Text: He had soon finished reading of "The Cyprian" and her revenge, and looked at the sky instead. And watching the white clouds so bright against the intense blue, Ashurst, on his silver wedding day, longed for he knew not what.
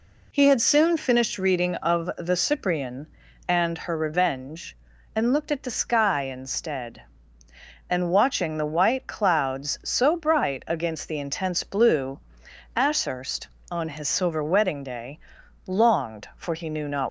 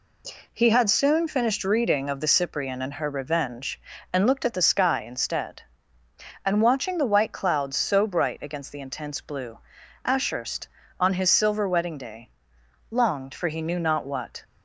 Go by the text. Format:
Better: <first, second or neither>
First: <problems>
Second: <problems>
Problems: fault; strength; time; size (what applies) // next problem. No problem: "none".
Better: second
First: stops before "what"; at 17.0 s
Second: none